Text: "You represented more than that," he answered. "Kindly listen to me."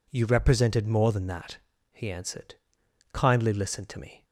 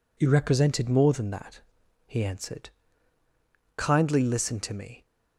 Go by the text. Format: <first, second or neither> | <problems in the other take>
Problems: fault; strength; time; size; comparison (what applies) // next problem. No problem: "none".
neither | none